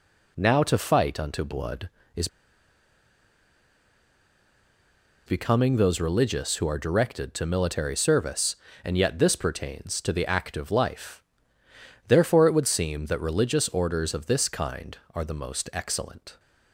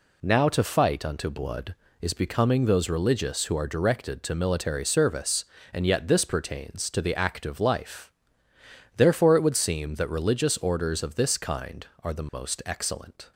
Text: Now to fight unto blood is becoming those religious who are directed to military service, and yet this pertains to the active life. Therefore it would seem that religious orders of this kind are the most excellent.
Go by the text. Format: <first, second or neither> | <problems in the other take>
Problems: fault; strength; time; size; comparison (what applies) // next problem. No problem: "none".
second | pauses between "is" and "becoming"; strong; at 2.2 s; 2.9 s long